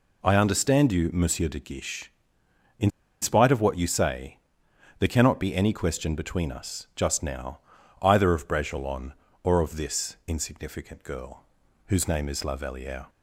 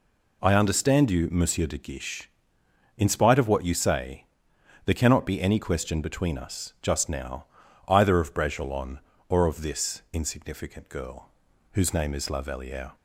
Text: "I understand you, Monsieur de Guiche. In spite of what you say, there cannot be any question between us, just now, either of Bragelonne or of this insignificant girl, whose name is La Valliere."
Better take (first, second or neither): second